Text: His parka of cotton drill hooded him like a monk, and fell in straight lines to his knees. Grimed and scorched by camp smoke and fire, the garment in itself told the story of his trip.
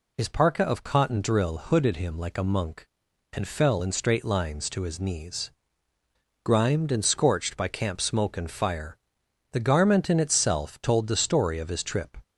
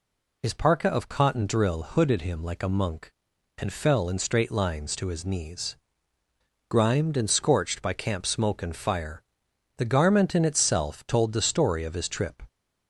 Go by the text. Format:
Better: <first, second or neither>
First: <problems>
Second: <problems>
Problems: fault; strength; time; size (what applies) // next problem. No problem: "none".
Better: neither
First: none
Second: none